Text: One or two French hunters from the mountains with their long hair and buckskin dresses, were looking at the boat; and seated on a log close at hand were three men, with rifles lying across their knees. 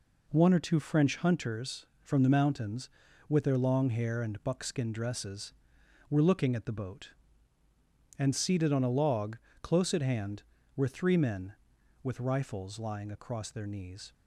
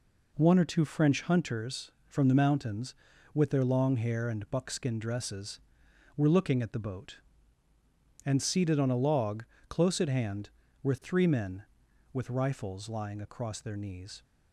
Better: neither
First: pauses between "log" and "close"; slight; at 9.3 s; 0.26 s long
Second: pauses between "log" and "close"; slight; at 9.4 s; 0.26 s long

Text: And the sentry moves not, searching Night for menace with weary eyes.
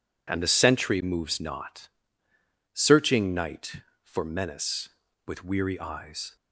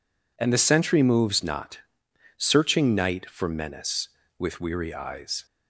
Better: neither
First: none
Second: none

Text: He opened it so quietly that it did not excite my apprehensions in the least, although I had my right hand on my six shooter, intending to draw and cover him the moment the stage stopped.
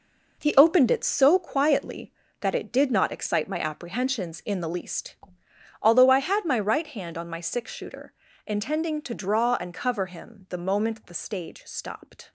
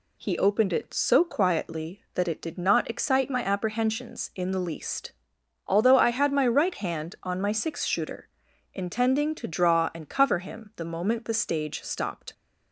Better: second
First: gets quieter; strong; throughout; 9.5 dB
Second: none

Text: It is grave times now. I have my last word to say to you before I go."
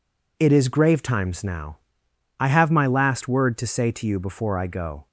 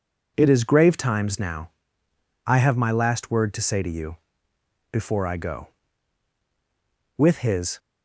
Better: first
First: none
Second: pauses between "you" and "before"; noticeable; at 4.1 s; 0.74 s long // goes on to say "With his"; noticeable; from 7.1 s on; 0.62 s long

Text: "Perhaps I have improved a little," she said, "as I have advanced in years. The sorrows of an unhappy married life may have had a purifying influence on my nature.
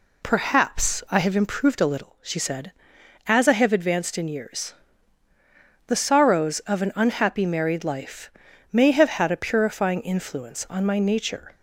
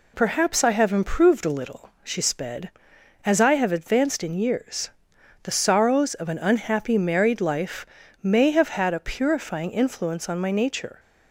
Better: first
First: pauses between "life" and "may"; at 8.2 s; 0.44 s long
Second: says "sped" for "said"; at 2.2 s // pauses between "life" and "may"; at 7.8 s; 0.38 s long

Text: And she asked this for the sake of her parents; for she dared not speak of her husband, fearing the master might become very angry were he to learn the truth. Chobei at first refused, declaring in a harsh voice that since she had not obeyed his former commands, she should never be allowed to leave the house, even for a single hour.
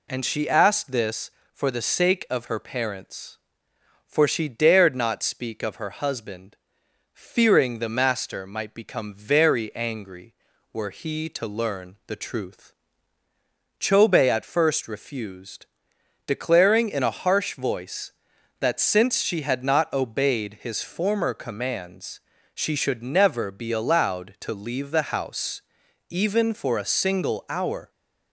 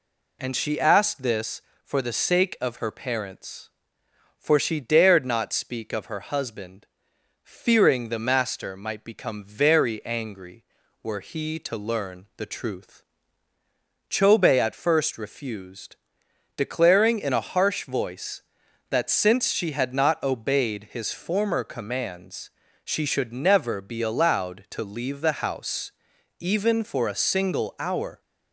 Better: neither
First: none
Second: none

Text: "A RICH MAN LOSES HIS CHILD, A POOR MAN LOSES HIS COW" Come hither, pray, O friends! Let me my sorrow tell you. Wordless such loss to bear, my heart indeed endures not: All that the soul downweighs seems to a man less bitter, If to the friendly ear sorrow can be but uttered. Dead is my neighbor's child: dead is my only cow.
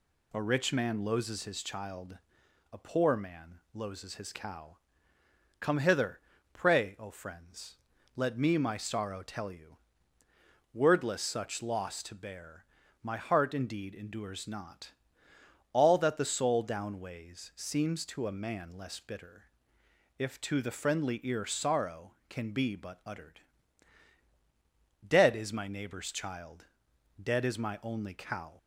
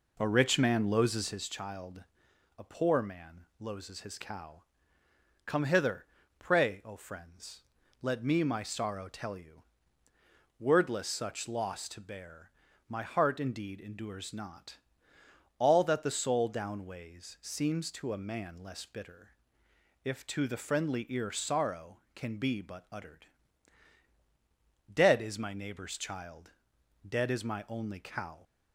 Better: first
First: pauses between "COW" and "Come"; noticeable; at 4.7 s; 0.82 s long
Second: starts louder than the rest; noticeable; until 1.5 s; 4 dB // pauses between "COW" and "Come"; noticeable; at 4.6 s; 0.82 s long

